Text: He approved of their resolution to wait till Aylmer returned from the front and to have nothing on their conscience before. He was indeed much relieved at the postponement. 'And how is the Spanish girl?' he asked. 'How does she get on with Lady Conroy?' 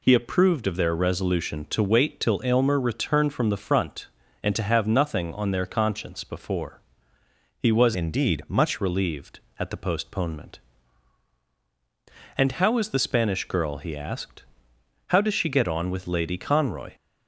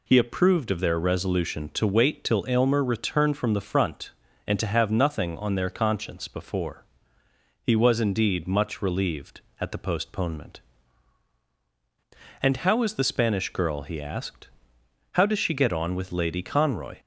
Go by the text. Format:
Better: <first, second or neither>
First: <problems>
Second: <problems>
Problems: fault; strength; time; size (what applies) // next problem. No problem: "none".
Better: second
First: changes voice from "indeed" to "much"; from 7.9 to 8.7 s; 0.8 s long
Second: none